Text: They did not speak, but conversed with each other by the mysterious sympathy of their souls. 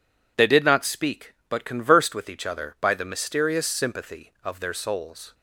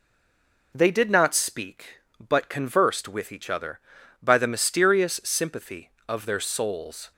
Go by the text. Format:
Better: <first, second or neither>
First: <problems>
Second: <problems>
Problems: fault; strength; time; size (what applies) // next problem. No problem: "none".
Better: first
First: none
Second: stays silent before the first word; slight; until 0.7 s; 0.7 s long